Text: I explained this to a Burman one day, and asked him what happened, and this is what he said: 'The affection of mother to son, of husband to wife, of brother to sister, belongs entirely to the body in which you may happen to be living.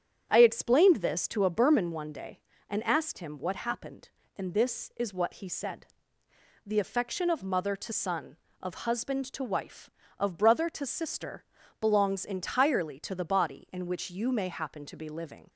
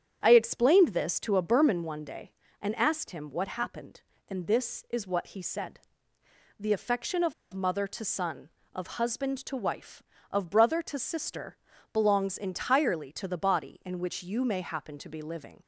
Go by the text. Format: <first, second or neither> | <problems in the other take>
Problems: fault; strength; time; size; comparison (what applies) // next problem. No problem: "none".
first | starts louder than the rest; strong; until 1.2 s; 8.5 dB; strong in the first // pauses between "of" and "mother"; slight; at 7.3 s; 0.20 s long